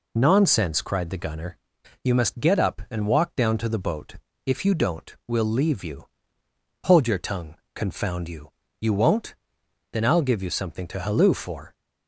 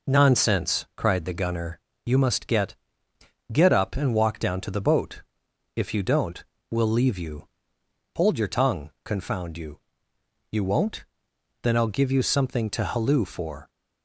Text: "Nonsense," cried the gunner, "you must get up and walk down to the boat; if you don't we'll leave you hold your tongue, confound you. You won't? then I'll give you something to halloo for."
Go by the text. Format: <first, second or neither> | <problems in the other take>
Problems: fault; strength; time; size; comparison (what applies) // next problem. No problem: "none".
first | says "get" twice; at 3.5 s // pauses between "don't" and "we'll"; slight; at 6.4 s; 0.26 s long // pauses between "you" and "hold"; noticeable; at 7.4 s; 0.70 s long; noticeable in the first